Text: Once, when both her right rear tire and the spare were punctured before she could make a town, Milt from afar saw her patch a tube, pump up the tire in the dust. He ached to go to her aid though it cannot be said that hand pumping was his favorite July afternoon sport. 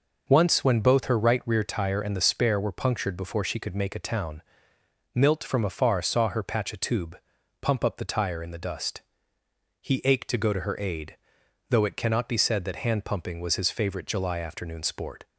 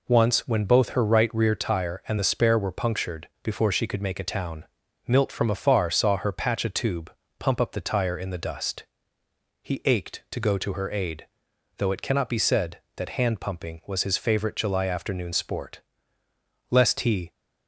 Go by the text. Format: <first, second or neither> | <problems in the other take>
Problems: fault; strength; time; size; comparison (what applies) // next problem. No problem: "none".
first | pauses between "punctured" and "before"; slight; at 3.2 s; 0.16 s long // pauses between "aid" and "though"; noticeable; at 11.2 s; 0.52 s long; noticeable in the first // goes on to say "Lest he"; noticeable; from 16.6 s on; 0.62 s long